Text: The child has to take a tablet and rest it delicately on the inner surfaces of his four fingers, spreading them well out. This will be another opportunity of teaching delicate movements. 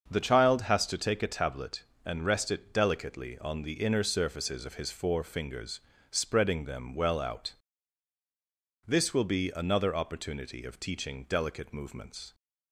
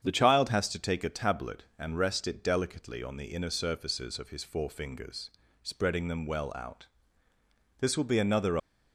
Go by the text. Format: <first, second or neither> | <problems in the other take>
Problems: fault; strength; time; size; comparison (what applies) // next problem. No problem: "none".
first | starts louder than the rest; strong; until 1.0 s; 8 dB; also in the first // stops before "opportunity of teaching delicate movements"; at 8.5 s